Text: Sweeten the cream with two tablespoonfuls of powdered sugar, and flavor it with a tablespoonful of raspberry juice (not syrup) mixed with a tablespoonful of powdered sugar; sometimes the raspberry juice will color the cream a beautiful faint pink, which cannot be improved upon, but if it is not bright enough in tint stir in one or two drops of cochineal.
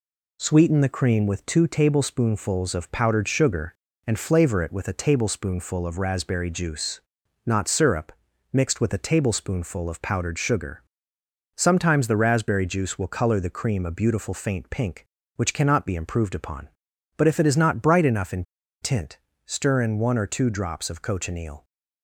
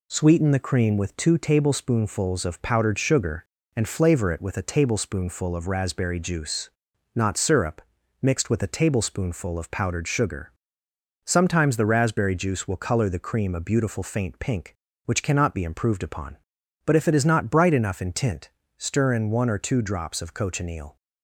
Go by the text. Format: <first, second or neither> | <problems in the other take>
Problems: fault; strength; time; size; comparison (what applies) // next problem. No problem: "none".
second | pauses between "in" and "tint"; at 18.4 s; 0.39 s long // pauses between "tint" and "stir"; slight; at 19.1 s; 0.28 s long; slight in the second